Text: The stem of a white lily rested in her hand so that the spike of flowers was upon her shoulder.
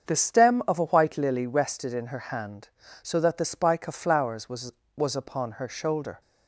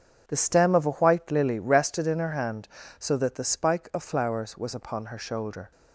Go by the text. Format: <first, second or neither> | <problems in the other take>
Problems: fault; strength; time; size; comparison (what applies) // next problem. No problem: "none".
second | starts louder than the rest; until 1.1 s; 7 dB; strong in the second // says "was" twice; at 4.9 s